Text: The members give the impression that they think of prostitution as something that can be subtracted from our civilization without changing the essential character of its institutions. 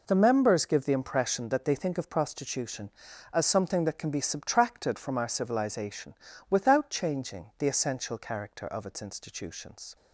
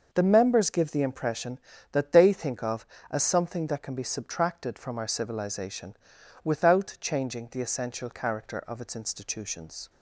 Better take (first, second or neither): first